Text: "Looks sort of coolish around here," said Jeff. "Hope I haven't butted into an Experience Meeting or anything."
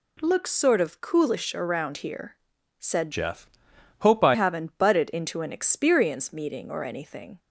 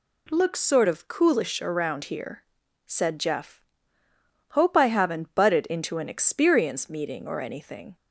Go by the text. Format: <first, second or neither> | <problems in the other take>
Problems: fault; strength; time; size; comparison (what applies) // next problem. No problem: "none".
second | changes voice from "Jeff" to "I"; from 3.1 to 4.3 s; 1.2 s long